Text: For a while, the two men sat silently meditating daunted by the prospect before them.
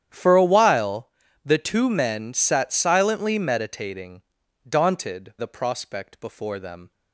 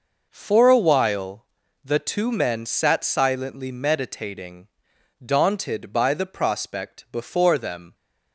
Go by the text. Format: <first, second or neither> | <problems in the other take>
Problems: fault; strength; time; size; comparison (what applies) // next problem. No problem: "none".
second | starts louder than the rest; strong; until 1.4 s; 9.5 dB // pauses between "meditating" and "daunted"; noticeable; at 4.2 s; 0.48 s long; noticeable in the second // skips "by"; at 5.3 s